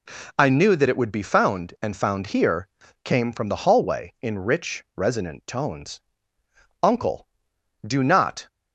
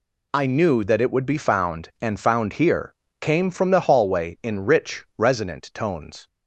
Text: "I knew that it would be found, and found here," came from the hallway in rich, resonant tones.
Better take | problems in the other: second | goes on to say "Uncle do not"; from 6.8 s on; 1.6 s long

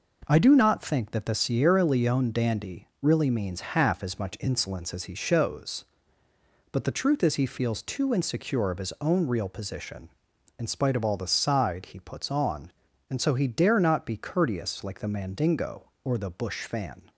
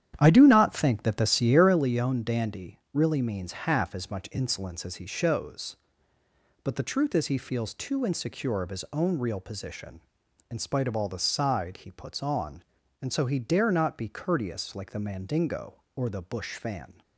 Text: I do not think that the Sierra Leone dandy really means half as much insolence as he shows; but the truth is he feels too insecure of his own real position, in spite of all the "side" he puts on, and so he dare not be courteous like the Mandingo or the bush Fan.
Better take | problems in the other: first | starts louder than the rest; strong; until 1.8 s; 10 dB

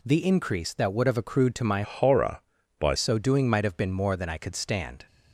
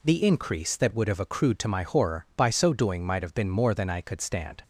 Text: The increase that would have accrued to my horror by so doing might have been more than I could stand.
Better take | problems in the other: second | changes voice from "horror" to "by"; from 1.8 to 2.9 s; 1.1 s long

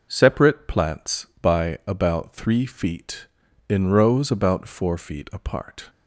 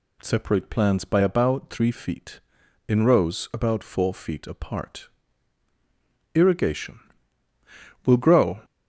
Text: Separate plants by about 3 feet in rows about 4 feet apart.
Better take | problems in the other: first | goes on to say "Irrigation Will grow"; strong; from 6.3 s on; 2.2 s long

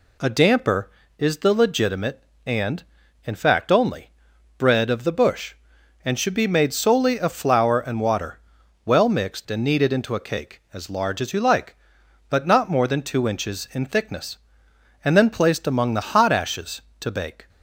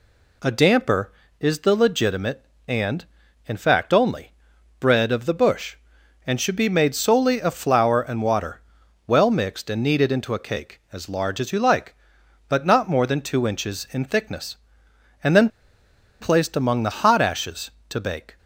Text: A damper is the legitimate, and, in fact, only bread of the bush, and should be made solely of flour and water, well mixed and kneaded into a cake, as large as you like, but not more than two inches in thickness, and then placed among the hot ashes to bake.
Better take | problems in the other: first | pauses between "only" and "bread"; noticeable; at 4.3 s; 0.48 s long; noticeable in the first // pauses between "then" and "placed"; noticeable; at 15.4 s; 0.71 s long

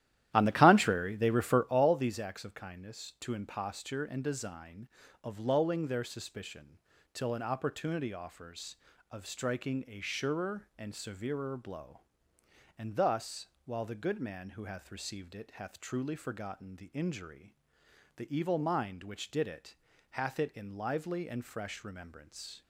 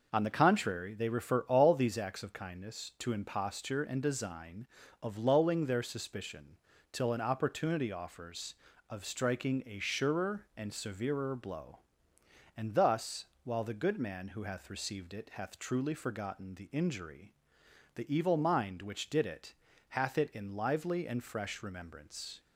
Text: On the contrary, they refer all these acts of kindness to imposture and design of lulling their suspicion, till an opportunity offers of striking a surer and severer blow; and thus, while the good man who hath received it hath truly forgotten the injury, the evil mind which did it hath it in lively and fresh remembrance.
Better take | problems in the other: second | starts louder than the rest; strong; until 1.8 s; 12.5 dB // pauses between "it" and "hath"; at 19.7 s; 0.38 s long; also in the second

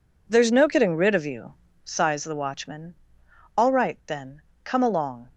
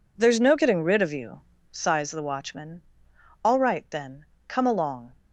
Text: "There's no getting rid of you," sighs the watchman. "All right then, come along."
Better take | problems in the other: neither | none

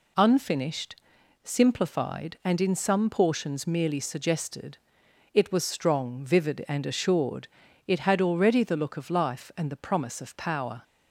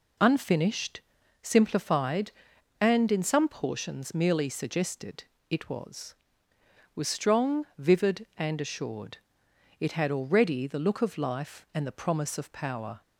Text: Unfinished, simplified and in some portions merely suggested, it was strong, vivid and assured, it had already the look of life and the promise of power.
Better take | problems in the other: first | says "was" twice; at 6.9 s

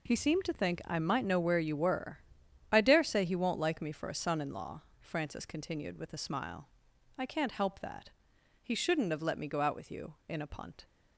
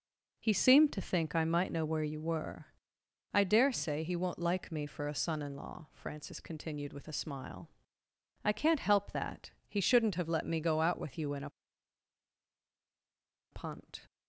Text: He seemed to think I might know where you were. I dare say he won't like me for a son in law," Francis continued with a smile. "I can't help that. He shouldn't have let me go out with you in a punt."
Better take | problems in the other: first | pauses between "a" and "punt"; strong; at 11.5 s; 2.0 s long

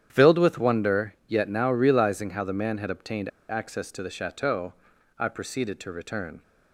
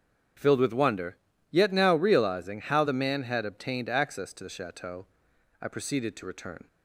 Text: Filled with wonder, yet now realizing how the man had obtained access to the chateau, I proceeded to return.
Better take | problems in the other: second | starts louder than the rest; strong; until 1.1 s; 9.5 dB; strong in the second // pauses between "obtained" and "access"; slight; at 3.2 s; 0.20 s long

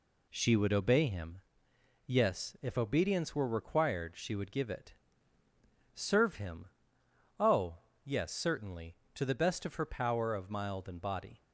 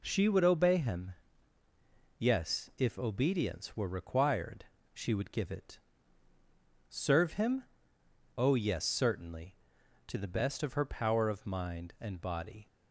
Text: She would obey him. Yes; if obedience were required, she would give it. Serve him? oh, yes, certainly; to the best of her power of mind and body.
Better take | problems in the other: second | says "mild" for "mind"; at 10.4 s

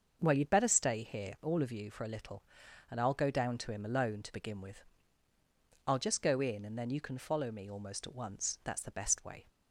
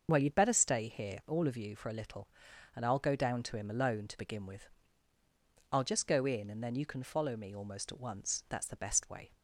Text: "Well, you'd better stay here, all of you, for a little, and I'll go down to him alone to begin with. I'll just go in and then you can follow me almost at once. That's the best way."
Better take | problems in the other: first | loses the start of "Well"; at 0.0 s; 25 ms // starts louder than the rest; until 1.0 s; 6.5 dB; also in the first

